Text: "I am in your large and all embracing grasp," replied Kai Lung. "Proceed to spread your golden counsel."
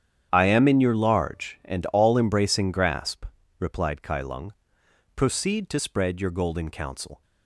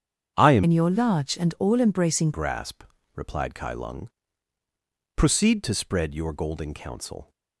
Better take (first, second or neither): first